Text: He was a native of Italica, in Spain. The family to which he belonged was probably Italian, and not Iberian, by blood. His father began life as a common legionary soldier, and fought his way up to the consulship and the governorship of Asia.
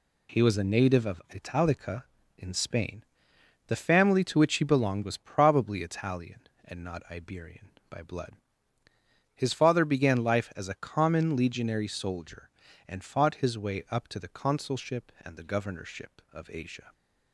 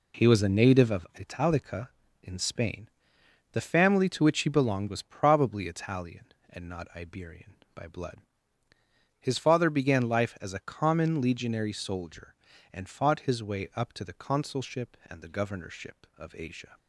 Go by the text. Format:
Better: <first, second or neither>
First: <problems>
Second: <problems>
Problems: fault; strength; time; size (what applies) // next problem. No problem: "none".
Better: first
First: none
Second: starts louder than the rest; slight; until 1.2 s; 3 dB